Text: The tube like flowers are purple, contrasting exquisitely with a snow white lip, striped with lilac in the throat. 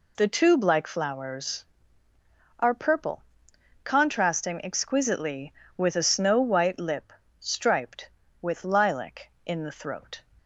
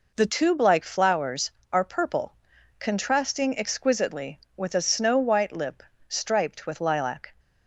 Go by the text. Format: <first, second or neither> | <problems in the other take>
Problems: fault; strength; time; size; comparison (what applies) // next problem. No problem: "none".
first | stops before "in the throat"; at 7.3 s